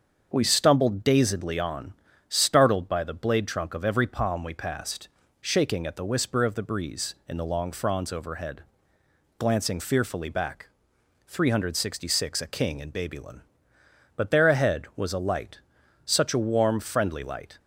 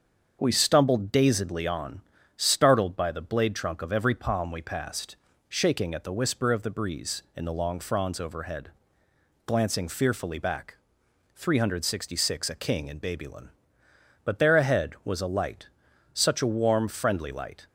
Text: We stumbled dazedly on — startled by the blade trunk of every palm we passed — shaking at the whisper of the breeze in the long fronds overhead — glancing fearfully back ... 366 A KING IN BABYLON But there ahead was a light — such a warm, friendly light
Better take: neither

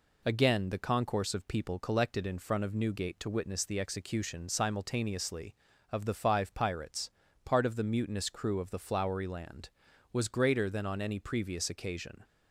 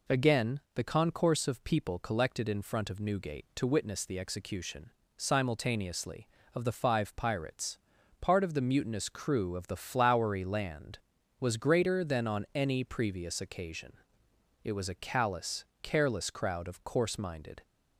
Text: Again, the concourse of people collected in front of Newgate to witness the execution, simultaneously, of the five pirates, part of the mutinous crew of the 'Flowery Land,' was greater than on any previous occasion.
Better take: first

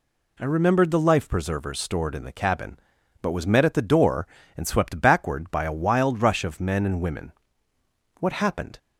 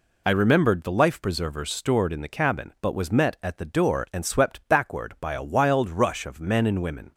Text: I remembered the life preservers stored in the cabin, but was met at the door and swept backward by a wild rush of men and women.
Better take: second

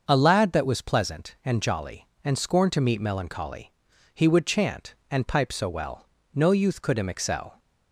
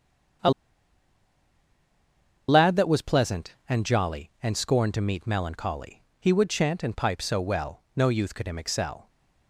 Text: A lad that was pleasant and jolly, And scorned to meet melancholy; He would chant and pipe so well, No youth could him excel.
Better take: first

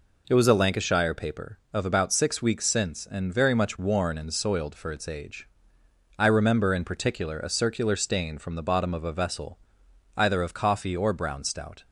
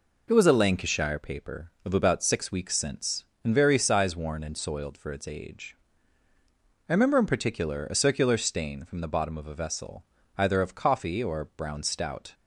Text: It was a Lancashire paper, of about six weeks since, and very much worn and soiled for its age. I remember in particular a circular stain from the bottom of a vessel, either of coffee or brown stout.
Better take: first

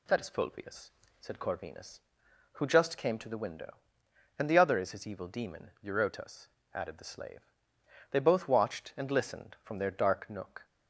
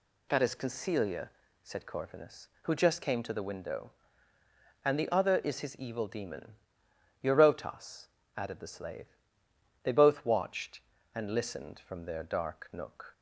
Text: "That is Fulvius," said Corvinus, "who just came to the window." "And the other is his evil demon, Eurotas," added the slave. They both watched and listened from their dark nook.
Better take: first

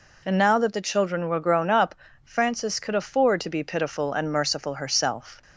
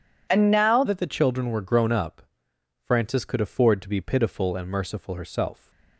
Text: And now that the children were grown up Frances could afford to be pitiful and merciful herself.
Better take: first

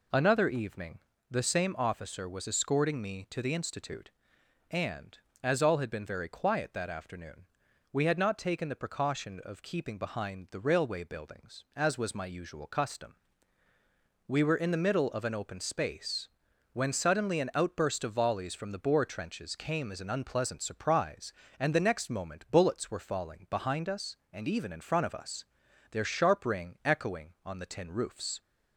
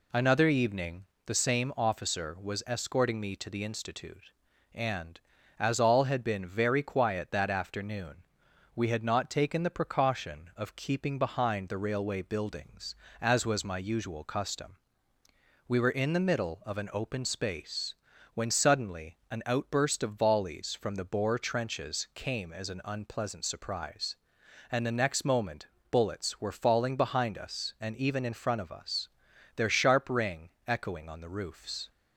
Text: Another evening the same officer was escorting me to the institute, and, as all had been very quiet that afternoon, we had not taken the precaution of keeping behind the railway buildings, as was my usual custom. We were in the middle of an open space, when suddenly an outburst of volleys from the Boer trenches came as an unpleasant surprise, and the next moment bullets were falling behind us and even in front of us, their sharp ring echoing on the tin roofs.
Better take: first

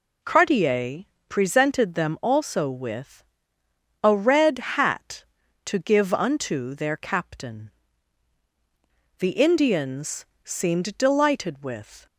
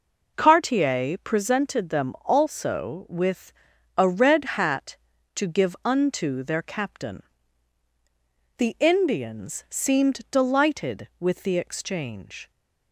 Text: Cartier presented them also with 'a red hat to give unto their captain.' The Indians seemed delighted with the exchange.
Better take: second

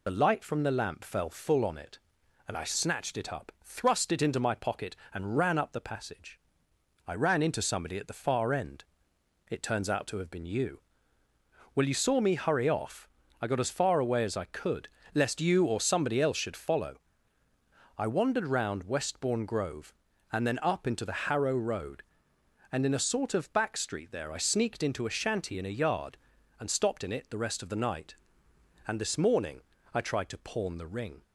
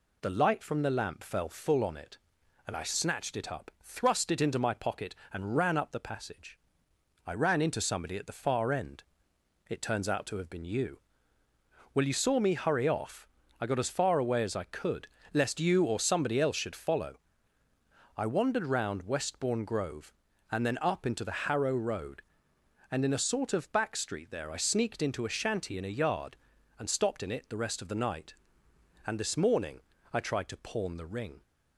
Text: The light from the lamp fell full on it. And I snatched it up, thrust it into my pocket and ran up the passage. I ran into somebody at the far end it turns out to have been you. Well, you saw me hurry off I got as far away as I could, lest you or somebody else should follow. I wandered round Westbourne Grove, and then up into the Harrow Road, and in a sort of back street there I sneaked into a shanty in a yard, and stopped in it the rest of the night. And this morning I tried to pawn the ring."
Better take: second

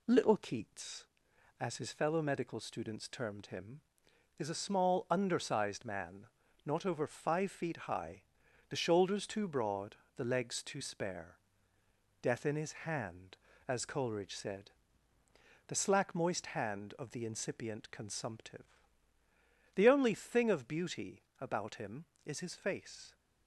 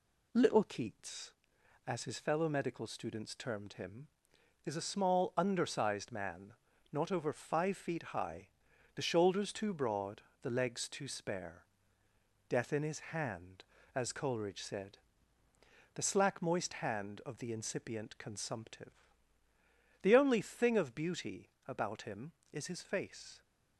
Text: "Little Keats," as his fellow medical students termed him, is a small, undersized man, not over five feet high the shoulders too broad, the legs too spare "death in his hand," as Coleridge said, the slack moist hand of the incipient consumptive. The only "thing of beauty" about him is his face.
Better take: neither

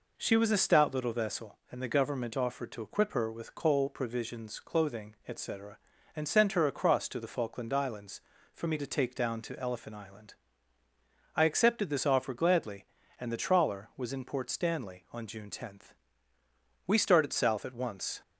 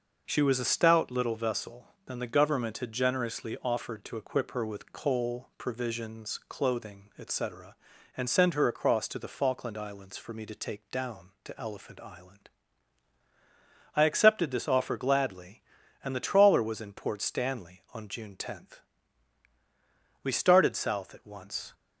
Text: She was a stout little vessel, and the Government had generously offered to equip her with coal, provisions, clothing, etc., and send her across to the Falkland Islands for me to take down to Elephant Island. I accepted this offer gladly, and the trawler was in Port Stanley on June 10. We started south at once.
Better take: second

